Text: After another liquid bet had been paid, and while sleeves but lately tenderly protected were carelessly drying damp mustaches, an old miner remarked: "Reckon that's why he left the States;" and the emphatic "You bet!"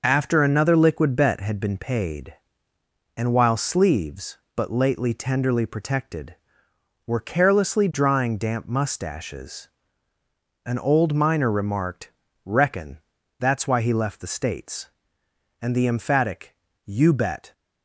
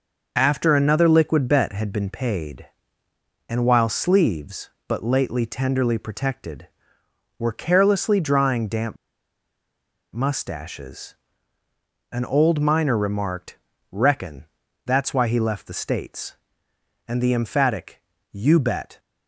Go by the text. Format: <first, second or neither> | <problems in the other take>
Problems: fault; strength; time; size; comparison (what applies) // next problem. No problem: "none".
first | pauses between "damp" and "mustaches"; at 8.9 s; 1.1 s long // pauses between "Reckon" and "that's"; at 14.4 s; 0.42 s long; also in the first // pauses between "emphatic" and "You"; slight; at 18.0 s; 0.30 s long; slight in the first